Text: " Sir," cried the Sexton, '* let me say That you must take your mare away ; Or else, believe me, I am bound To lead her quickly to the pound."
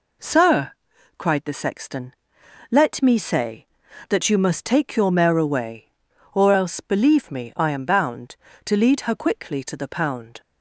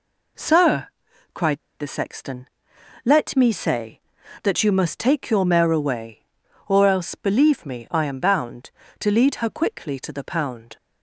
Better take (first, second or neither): first